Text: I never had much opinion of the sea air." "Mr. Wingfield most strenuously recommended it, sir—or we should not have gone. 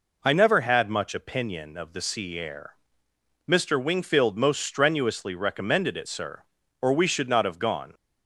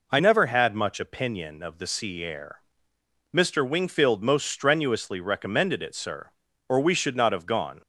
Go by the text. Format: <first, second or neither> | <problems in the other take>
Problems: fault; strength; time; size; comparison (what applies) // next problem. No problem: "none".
neither | none